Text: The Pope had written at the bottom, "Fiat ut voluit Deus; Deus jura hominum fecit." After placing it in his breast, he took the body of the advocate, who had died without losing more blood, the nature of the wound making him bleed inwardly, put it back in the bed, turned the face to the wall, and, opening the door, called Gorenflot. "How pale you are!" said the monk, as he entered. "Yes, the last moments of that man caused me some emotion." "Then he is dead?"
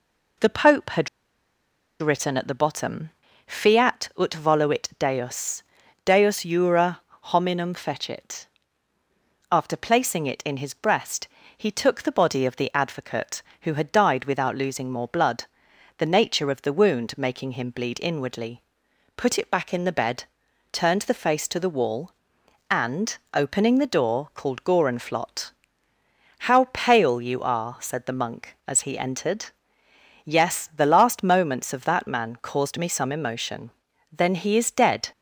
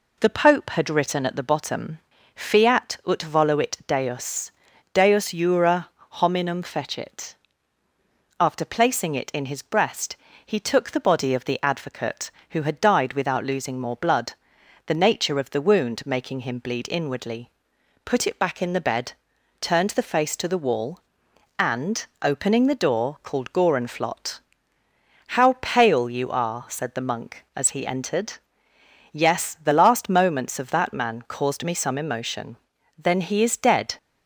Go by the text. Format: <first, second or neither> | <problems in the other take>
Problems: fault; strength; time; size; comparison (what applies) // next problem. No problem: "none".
second | pauses between "had" and "written"; noticeable; at 1.0 s; 0.92 s long // pauses between "jura" and "hominum"; slight; at 7.0 s; 0.24 s long; slight in the second